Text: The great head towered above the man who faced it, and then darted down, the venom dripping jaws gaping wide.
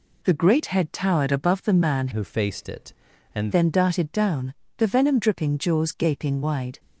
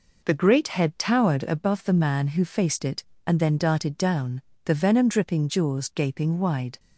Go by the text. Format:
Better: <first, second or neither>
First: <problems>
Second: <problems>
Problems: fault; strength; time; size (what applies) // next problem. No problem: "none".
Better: second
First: changes voice from "who" to "and"; from 2.1 to 3.5 s; 1.4 s long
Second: none